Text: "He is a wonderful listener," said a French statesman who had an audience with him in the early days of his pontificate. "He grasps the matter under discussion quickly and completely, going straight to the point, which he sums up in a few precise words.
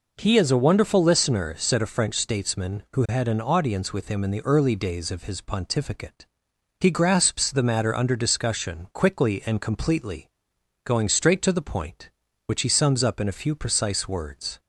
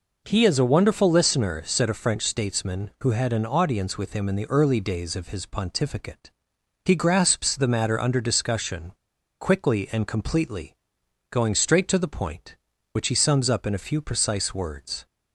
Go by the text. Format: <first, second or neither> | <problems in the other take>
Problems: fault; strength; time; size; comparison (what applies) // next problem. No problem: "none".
first | pauses between "discussion" and "quickly"; noticeable; at 8.9 s; 0.47 s long